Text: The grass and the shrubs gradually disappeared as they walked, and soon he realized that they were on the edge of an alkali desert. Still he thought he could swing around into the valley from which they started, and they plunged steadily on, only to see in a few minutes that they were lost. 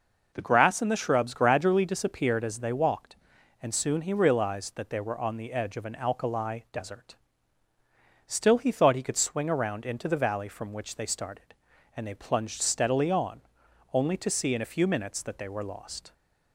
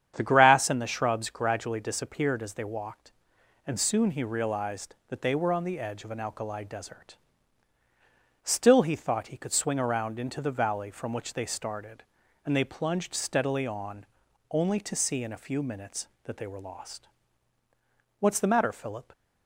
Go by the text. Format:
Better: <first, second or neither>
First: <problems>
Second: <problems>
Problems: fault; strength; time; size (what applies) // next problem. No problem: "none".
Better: first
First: none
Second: starts louder than the rest; strong; until 1.1 s; 8.5 dB // goes on to say "What's the matter Philip"; noticeable; from 18.1 s on; 0.92 s long